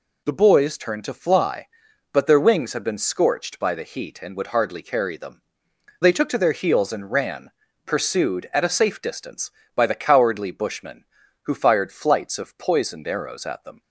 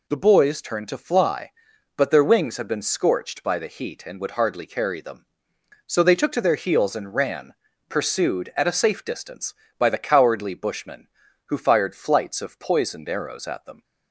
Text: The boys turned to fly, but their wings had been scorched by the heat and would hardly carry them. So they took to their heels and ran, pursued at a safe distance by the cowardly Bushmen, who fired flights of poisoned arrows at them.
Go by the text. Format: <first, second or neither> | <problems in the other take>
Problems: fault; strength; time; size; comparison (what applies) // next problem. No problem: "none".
second | skips "So"; at 5.7 s